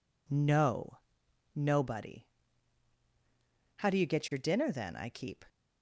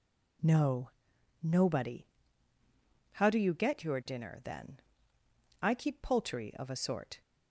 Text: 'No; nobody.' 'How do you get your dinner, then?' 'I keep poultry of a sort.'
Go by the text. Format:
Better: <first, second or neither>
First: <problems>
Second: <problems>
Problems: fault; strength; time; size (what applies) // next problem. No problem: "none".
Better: second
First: stops before "poultry of a sort"; at 5.4 s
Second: none